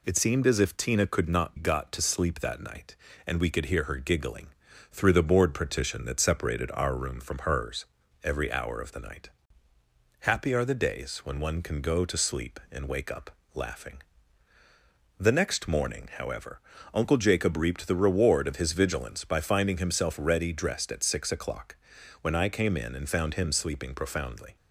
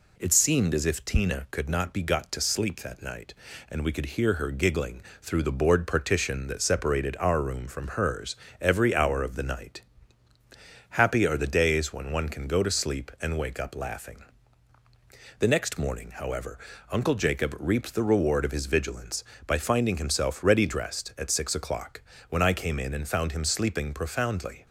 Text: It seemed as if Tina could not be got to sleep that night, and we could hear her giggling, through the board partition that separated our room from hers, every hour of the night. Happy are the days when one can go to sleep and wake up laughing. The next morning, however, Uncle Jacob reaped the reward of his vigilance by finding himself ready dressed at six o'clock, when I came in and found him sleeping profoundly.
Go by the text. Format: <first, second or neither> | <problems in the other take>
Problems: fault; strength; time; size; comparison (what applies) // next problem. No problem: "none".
second | skips "be"; at 1.5 s // pauses between "up" and "laughing"; slight; at 13.3 s; 0.24 s long